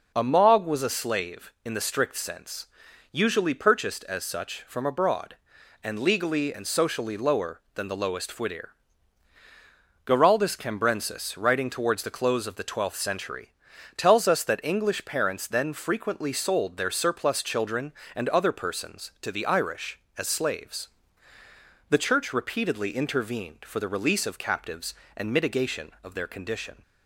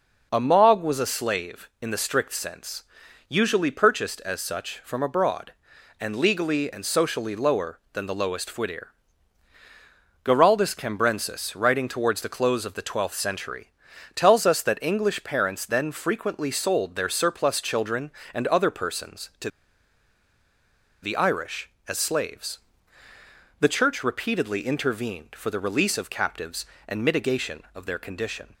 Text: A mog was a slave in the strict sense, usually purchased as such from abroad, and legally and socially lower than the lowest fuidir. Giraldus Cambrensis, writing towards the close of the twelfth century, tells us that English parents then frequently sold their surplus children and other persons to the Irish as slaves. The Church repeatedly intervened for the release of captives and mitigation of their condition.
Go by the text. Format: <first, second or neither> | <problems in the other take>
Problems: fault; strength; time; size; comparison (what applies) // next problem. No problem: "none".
first | pauses between "to" and "the"; strong; at 19.4 s; 1.5 s long